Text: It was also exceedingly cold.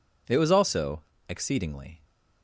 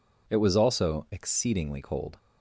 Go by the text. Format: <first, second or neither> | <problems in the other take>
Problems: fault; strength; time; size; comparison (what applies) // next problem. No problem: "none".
second | pauses between "also" and "exceedingly"; slight; at 1.0 s; 0.26 s long // stops before "cold"; at 2.0 s